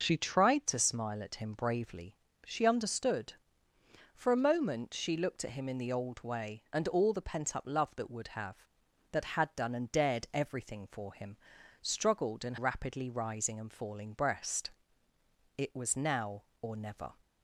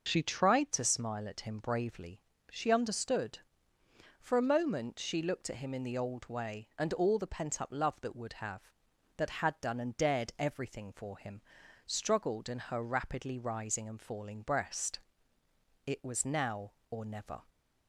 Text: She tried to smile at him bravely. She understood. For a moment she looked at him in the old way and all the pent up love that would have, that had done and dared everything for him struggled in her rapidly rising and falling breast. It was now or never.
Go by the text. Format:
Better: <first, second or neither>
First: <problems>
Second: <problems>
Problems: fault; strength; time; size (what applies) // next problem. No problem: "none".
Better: second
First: pauses between "him" and "struggled"; noticeable; at 11.3 s; 0.46 s long // skips "her"; at 12.5 s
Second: pauses between "him" and "struggled"; noticeable; at 11.4 s; 0.46 s long